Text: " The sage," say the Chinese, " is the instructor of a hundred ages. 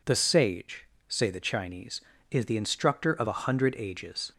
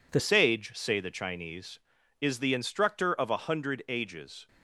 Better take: first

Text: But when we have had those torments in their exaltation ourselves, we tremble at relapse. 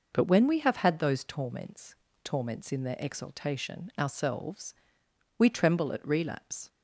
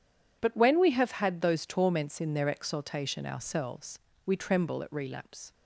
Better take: second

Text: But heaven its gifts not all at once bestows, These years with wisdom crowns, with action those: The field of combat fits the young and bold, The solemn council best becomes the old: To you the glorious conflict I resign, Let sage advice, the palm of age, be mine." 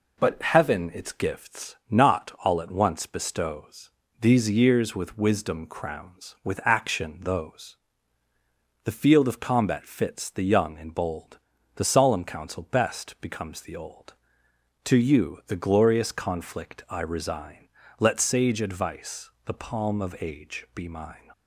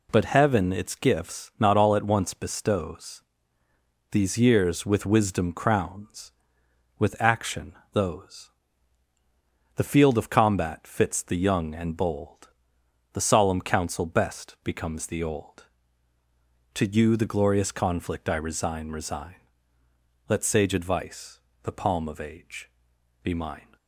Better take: first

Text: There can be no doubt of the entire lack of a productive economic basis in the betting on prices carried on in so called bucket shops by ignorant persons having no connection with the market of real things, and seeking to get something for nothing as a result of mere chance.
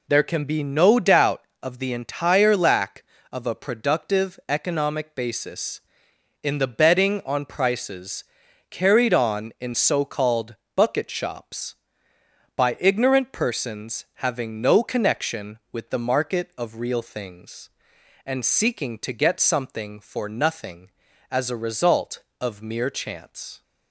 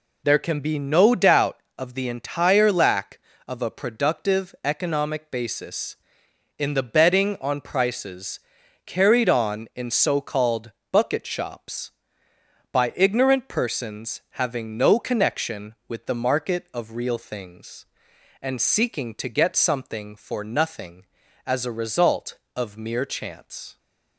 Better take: neither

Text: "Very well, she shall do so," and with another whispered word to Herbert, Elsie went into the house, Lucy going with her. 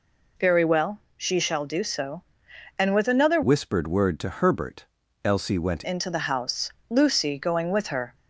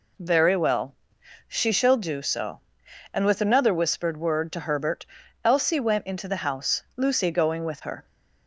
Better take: second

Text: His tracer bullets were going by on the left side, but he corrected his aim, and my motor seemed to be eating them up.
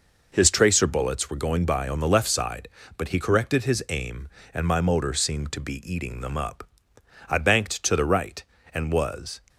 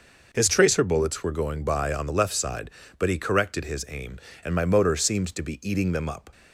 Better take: second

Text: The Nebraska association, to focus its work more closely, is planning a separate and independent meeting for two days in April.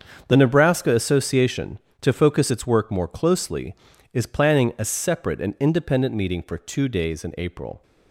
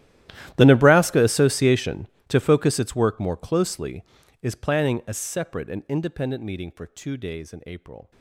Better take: first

